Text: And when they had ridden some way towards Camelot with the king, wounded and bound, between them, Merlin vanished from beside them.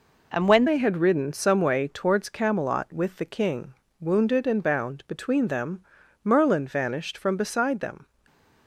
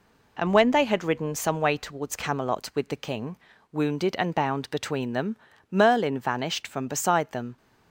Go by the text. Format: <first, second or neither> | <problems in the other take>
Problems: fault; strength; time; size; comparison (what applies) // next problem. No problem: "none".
second | changes voice at "they"; from 0.6 s on; 7.4 s long // stays silent after the last word; slight; from 8.0 s on; 0.6 s long